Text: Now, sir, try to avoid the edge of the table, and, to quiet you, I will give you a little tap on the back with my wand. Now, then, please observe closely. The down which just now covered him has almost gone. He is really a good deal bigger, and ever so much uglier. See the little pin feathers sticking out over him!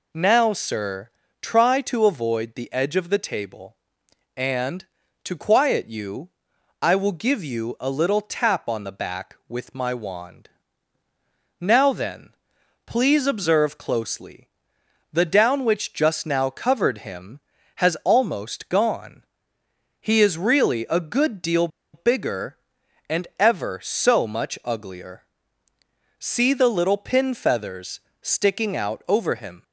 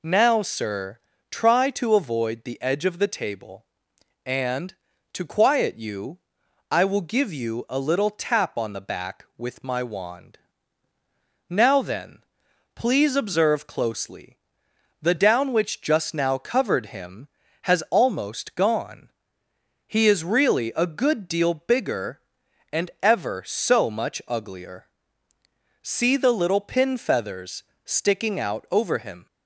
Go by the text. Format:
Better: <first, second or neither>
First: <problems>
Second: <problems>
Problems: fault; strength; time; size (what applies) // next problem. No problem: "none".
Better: second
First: pauses between "deal" and "bigger"; slight; at 21.6 s; 0.26 s long // pauses between "feathers" and "sticking"; slight; at 27.9 s; 0.22 s long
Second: pauses between "feathers" and "sticking"; slight; at 27.6 s; 0.22 s long